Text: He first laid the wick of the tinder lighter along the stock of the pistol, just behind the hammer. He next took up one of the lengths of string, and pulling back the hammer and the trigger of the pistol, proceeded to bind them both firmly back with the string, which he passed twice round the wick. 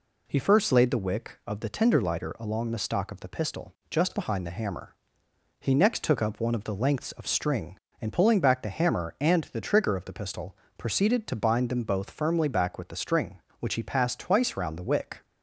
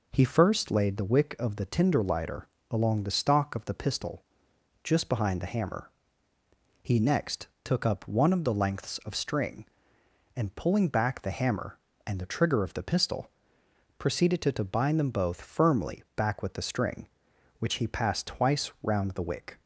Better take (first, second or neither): first